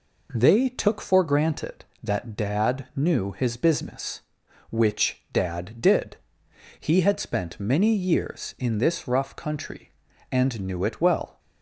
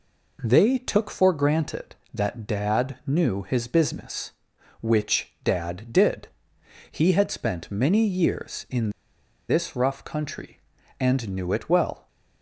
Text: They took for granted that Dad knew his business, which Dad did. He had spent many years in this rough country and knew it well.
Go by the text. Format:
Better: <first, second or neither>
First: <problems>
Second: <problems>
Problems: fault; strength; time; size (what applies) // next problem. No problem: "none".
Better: first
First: none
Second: pauses between "in" and "this"; noticeable; at 8.8 s; 0.59 s long